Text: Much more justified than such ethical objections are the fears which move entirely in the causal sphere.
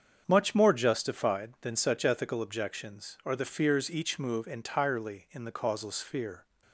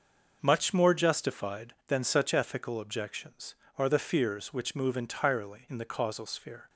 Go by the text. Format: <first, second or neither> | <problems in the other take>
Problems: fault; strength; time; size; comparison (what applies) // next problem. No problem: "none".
second | starts louder than the rest; strong; until 1.2 s; 7.5 dB; noticeable in the second // says "each" for "which"; at 3.9 s